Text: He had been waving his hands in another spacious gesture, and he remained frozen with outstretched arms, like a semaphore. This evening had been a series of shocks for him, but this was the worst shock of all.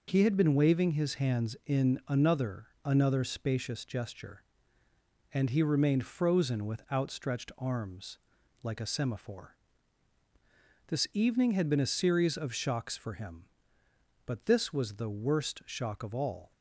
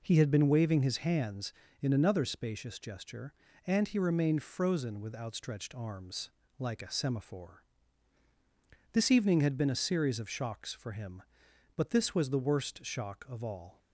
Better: second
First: says "another" twice; at 2.8 s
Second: none

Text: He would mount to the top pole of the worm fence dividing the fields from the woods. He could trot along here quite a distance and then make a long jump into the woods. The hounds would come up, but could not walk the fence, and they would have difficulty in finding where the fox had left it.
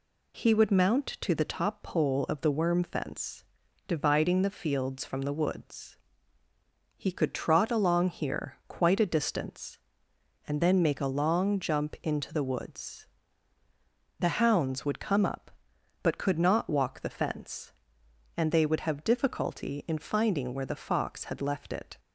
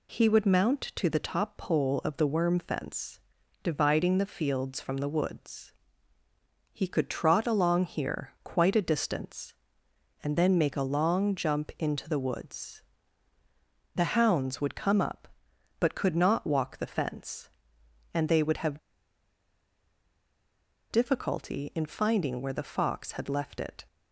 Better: first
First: pauses between "fence" and "dividing"; at 3.4 s; 0.42 s long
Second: pauses between "fence" and "dividing"; at 3.2 s; 0.42 s long // pauses between "have" and "difficulty"; strong; at 18.7 s; 2.1 s long

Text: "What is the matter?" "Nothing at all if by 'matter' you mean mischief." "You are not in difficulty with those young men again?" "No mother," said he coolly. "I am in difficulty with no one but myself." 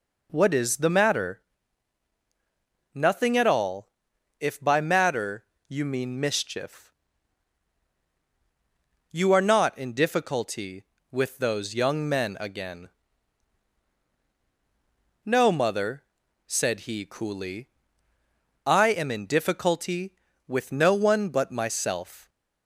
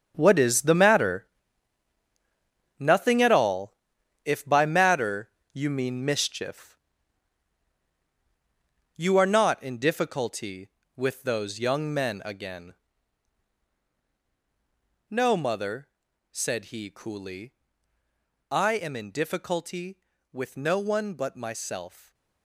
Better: first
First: pauses between "all" and "if"; noticeable; at 3.9 s; 0.48 s long // pauses between "matter" and "you"; slight; at 5.4 s; 0.22 s long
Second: gets quieter; strong; throughout; 11 dB // pauses between "all" and "if"; noticeable; at 3.7 s; 0.48 s long // pauses between "matter" and "you"; slight; at 5.2 s; 0.22 s long

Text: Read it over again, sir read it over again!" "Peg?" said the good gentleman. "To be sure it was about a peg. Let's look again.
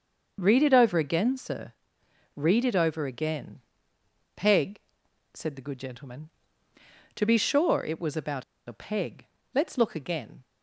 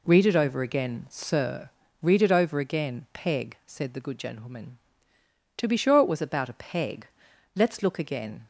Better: second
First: starts louder than the rest; until 1.4 s; 6 dB // pauses between "sir" and "read"; noticeable; at 1.7 s; 0.60 s long // pauses between "about" and "a"; slight; at 8.4 s; 0.24 s long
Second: pauses between "sir" and "read"; slight; at 1.6 s; 0.34 s long

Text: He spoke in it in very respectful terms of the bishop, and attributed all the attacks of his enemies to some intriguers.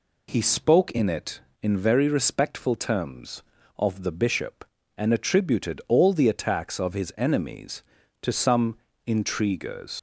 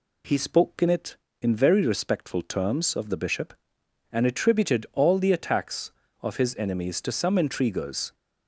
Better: second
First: pauses between "some" and "intriguers"; slight; at 8.7 s; 0.30 s long // leaves "intriguers" unfinished; at 9.9 s; 110 ms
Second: none

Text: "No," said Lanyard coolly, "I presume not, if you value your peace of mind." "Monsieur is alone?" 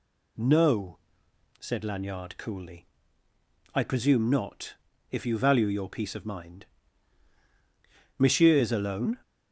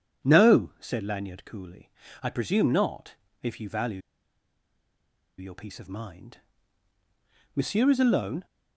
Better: first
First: none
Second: pauses between "value" and "your"; strong; at 4.0 s; 1.3 s long

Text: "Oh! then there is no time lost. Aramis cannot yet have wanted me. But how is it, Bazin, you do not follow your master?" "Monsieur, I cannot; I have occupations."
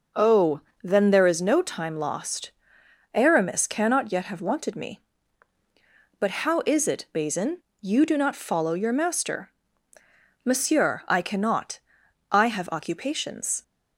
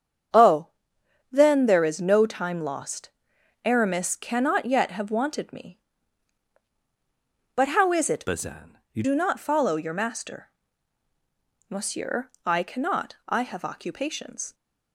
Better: first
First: none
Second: starts louder than the rest; strong; until 1.9 s; 8 dB // changes voice from "Bazin" to "you"; from 8.2 to 9.0 s; 0.8 s long

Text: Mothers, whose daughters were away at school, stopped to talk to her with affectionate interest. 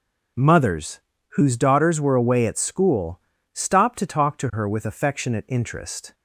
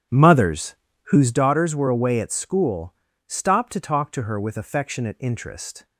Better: first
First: none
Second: starts louder than the rest; strong; until 1.5 s; 9.5 dB

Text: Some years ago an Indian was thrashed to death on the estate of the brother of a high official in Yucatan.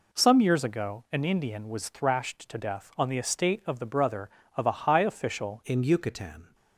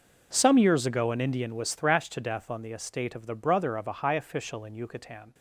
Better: second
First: changes voice at "in"; from 5.6 s on; 0.9 s long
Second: none

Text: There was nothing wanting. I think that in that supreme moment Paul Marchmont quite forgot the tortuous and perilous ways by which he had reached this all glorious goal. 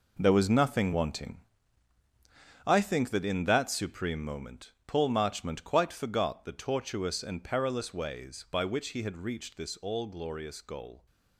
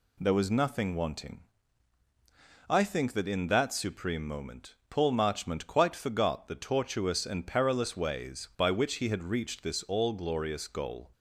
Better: second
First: gets quieter; strong; throughout; 10.5 dB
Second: none

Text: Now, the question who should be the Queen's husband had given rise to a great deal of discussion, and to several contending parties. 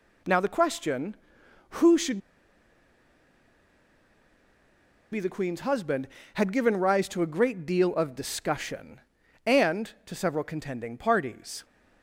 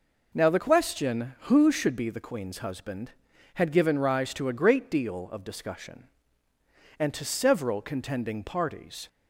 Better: second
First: pauses between "should" and "be"; strong; at 2.1 s; 2.9 s long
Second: none

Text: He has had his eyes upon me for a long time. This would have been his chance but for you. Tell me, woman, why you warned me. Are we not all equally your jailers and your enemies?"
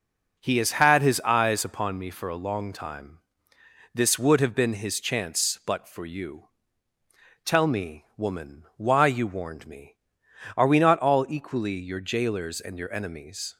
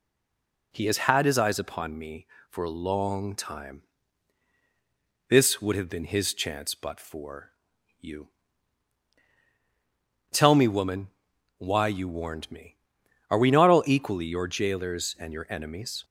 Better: first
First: none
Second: stays silent before the first word; slight; until 0.7 s; 0.7 s long // pauses between "for" and "you"; noticeable; at 7.5 s; 0.50 s long

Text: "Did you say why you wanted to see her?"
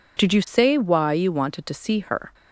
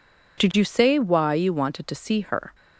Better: neither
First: none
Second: none

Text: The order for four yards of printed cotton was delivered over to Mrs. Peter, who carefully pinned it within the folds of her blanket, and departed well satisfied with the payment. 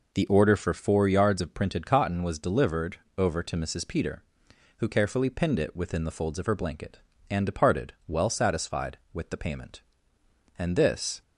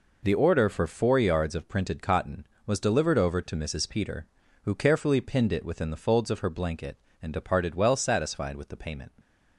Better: second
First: pauses between "delivered" and "over"; slight; at 2.9 s; 0.22 s long // goes on to say "And this"; noticeable; from 10.5 s on; 0.64 s long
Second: none

